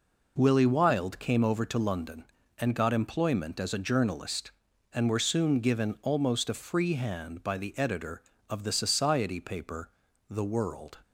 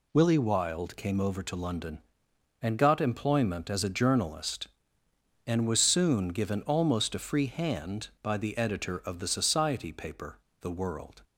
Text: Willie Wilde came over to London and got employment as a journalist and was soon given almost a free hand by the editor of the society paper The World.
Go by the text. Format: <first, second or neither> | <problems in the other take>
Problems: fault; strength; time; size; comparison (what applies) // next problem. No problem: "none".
second | says "were" for "was"; at 5.0 s // pauses between "paper" and "The"; at 9.8 s; 0.40 s long; slight in the second